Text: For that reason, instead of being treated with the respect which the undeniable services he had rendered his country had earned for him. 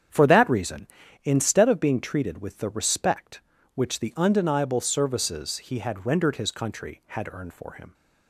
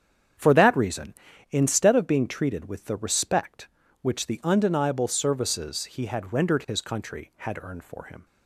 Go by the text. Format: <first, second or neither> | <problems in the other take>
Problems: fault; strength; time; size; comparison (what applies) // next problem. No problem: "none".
neither | starts louder than the rest; strong; the same in both